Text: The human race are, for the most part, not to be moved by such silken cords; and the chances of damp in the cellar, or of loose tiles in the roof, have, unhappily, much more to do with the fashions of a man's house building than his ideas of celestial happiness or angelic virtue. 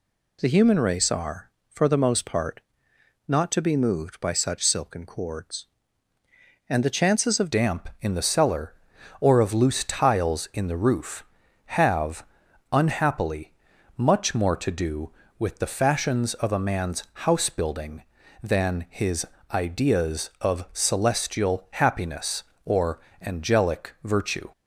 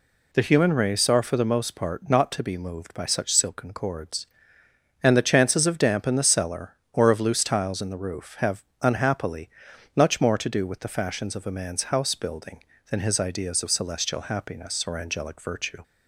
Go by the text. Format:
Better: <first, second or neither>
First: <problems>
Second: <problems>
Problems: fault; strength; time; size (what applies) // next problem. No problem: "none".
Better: second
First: changes voice at "damp"; from 7.5 s on; 16.9 s long // pauses between "his" and "ideas"; slight; at 19.2 s; 0.26 s long // pauses between "or" and "angelic"; slight; at 22.9 s; 0.22 s long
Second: none